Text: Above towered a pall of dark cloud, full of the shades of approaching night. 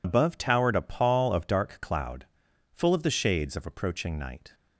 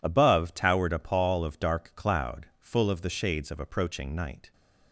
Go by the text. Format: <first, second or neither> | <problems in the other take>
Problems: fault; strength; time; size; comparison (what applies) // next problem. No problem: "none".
second | loses the start of "Above"; at 0.0 s; 80 ms